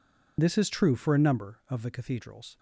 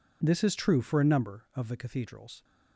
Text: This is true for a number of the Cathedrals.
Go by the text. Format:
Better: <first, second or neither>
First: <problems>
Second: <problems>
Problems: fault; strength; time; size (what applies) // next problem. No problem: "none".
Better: second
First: loses the start of "This"; at 0.3 s; 35 ms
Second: none